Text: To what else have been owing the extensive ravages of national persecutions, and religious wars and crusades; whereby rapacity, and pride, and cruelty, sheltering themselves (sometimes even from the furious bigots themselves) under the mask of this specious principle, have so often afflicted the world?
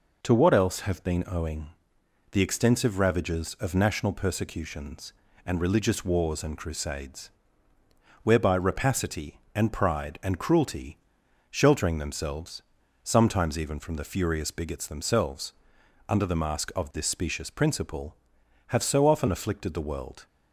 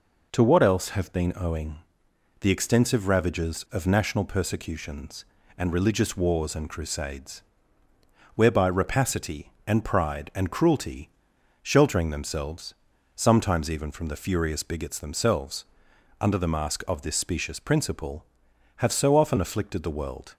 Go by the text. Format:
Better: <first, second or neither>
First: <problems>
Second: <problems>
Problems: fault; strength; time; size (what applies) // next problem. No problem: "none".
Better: neither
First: pauses between "owing" and "the"; noticeable; at 1.7 s; 0.62 s long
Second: pauses between "owing" and "the"; noticeable; at 1.7 s; 0.62 s long